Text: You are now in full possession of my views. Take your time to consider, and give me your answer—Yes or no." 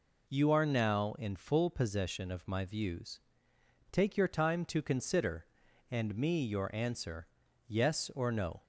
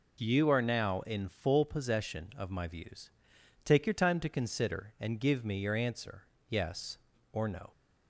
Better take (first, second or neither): second